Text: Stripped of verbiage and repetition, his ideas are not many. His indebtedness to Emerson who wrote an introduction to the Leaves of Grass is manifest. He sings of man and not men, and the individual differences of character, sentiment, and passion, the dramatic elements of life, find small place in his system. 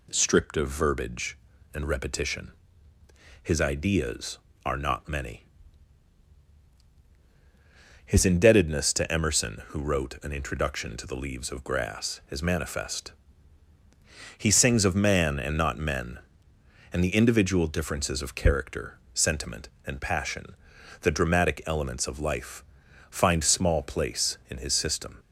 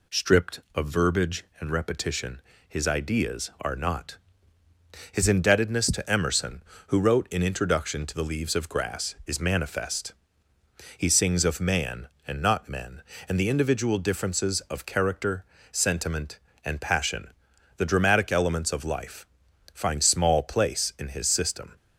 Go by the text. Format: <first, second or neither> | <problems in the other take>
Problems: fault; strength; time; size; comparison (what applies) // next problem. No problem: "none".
first | skips "many"; at 4.6 s